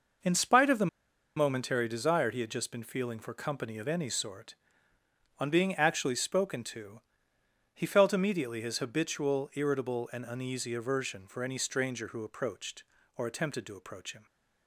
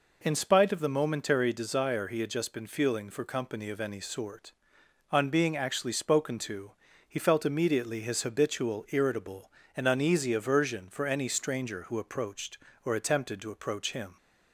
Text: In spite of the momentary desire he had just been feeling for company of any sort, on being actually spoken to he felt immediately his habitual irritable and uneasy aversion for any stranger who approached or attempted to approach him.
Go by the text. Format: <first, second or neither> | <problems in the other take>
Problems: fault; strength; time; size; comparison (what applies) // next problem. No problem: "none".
second | pauses between "the" and "momentary"; noticeable; at 0.8 s; 0.49 s long // pauses between "to" and "he"; noticeable; at 7.0 s; 0.70 s long; slight in the second